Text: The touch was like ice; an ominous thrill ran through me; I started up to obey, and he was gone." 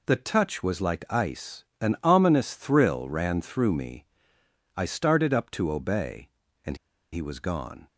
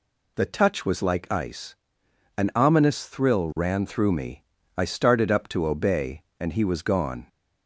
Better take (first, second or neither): second